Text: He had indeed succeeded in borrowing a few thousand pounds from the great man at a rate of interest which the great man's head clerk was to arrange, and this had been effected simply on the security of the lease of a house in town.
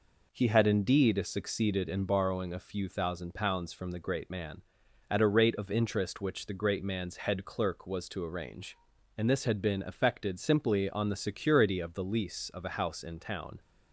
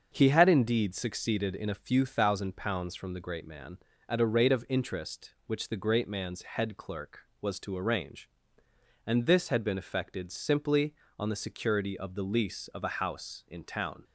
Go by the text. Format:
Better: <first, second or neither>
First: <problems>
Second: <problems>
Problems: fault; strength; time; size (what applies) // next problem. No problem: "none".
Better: first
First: none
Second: starts louder than the rest; until 1.1 s; 6.5 dB // skips "borrowing"; at 1.7 s